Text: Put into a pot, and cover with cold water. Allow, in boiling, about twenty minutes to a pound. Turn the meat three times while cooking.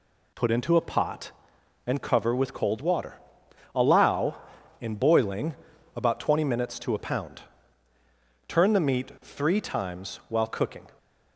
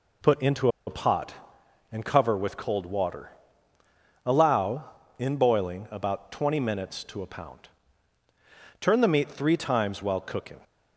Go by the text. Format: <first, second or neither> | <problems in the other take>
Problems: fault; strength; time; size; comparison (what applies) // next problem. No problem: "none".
first | pauses between "into" and "a"; slight; at 0.6 s; 0.18 s long